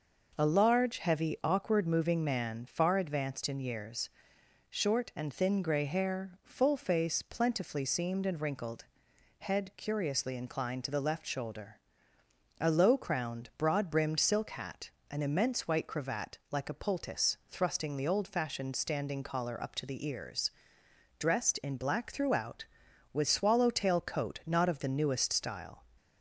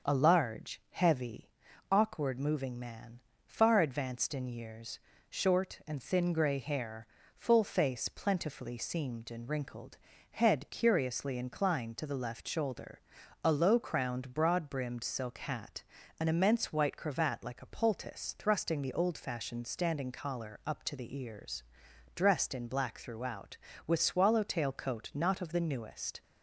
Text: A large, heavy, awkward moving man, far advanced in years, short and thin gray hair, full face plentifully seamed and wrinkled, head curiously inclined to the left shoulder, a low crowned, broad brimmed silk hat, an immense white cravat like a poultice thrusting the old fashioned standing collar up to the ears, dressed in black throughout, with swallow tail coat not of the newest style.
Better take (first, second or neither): first